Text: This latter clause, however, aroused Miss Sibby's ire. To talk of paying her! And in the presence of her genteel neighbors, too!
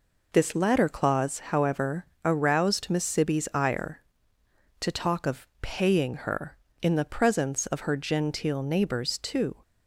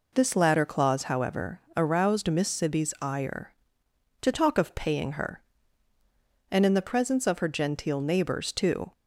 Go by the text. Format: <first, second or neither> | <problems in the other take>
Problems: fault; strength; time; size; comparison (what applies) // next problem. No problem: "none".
second | skips "And"; at 6.6 s